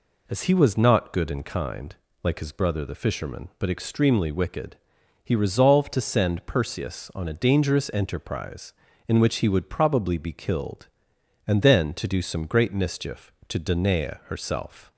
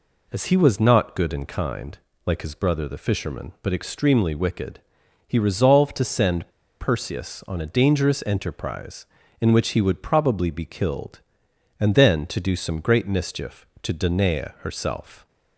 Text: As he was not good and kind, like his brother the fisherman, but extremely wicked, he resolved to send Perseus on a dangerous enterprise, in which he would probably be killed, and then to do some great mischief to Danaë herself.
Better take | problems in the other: first | pauses between "send" and "Perseus"; slight; at 6.5 s; 0.30 s long

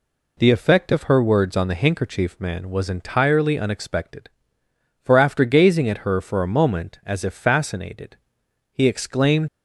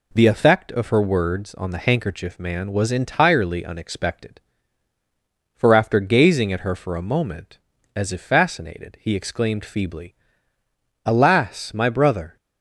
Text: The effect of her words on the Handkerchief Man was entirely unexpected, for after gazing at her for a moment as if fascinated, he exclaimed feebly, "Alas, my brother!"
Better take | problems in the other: second | stops before "feebly Alas my brother"; at 9.4 s

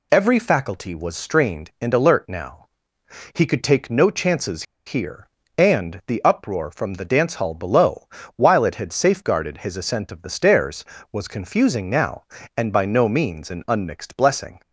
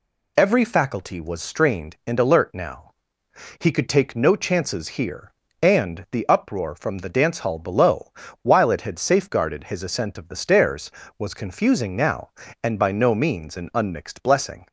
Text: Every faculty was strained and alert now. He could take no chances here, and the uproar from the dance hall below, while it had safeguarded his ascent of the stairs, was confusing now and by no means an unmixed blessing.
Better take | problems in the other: second | pauses between "chances" and "here"; slight; at 4.6 s; 0.22 s long

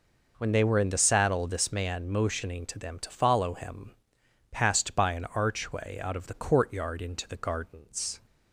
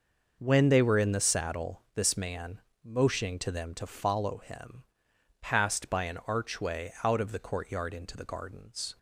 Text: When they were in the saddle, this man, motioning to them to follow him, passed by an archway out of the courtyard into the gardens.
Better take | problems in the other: neither | none

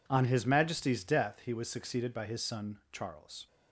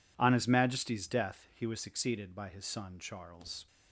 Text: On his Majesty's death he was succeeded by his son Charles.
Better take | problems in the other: neither | none

